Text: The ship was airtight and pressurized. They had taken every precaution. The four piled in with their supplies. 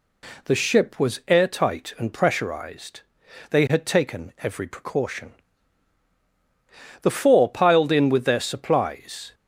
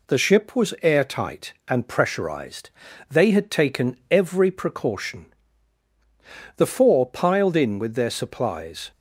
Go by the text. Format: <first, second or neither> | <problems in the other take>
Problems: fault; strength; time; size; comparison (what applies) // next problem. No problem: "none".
neither | none